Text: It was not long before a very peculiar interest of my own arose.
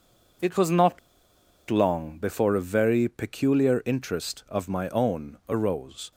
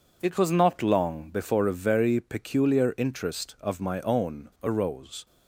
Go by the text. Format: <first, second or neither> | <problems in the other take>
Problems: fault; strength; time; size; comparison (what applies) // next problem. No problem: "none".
second | pauses between "not" and "long"; noticeable; at 0.9 s; 0.71 s long